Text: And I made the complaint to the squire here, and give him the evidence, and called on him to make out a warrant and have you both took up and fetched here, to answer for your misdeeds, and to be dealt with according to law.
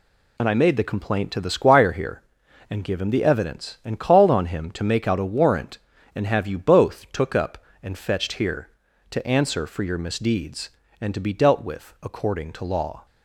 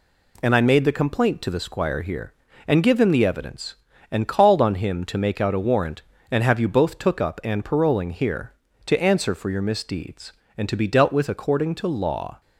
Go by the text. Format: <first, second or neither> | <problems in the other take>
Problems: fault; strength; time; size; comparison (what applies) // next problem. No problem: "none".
first | says "paroling" for "fetched"; at 7.6 s